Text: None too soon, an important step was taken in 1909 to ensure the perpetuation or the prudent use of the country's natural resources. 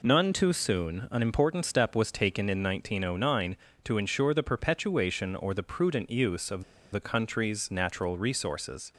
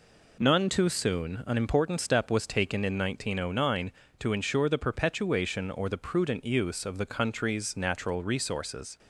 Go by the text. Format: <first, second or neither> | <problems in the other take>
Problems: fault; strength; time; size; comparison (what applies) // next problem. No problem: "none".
second | pauses between "of" and "the"; slight; at 6.6 s; 0.29 s long